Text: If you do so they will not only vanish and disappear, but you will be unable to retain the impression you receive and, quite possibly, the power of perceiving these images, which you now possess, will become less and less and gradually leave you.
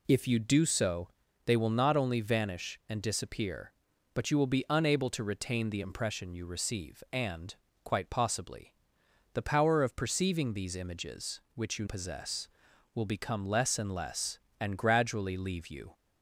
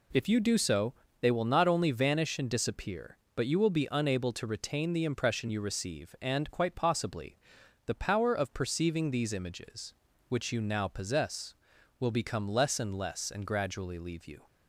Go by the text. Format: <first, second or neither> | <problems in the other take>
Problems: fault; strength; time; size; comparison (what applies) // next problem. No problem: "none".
second | pauses between "so" and "they"; at 1.0 s; 0.38 s long; slight in the second // skips "now"; at 11.8 s